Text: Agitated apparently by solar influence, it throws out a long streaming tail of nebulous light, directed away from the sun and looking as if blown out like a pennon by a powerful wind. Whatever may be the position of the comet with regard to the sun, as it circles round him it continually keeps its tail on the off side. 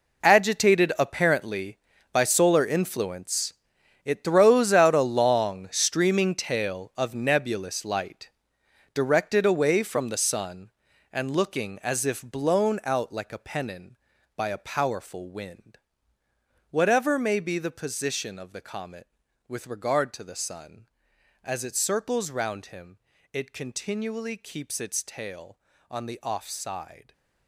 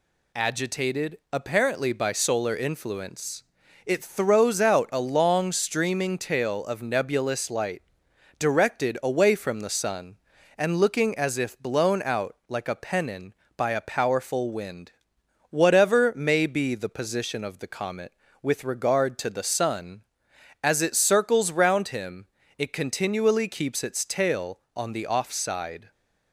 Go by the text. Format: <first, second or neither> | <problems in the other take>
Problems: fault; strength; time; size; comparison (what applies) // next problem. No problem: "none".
second | gets quieter; strong; throughout; 14 dB // pauses between "him" and "it"; slight; at 22.9 s; 0.34 s long; slight in the second